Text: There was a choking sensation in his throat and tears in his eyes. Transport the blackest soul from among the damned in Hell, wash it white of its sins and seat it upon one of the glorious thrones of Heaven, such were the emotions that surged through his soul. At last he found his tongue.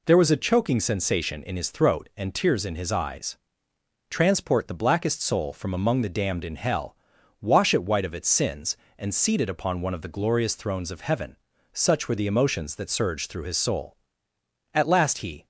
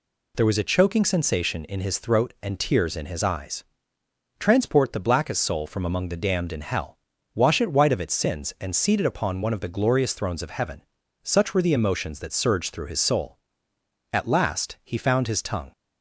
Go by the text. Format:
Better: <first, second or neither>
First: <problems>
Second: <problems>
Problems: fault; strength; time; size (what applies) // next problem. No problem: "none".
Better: second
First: stops before "found his tongue"; at 15.4 s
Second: none